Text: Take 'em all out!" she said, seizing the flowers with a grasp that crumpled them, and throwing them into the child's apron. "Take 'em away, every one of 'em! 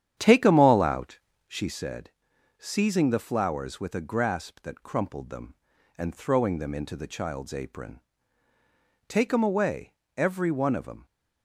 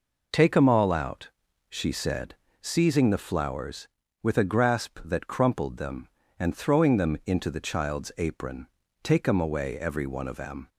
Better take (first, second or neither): second